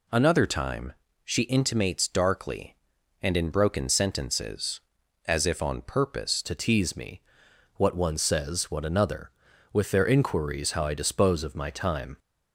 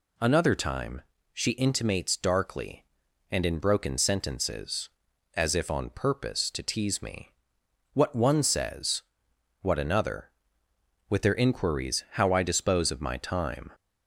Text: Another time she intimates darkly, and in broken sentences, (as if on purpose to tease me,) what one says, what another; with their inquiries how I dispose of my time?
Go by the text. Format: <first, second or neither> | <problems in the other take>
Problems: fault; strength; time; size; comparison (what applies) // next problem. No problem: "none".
second | pauses between "time" and "she"; slight; at 0.9 s; 0.32 s long; slight in the second // changes voice at "to"; from 6.4 s on; 5.7 s long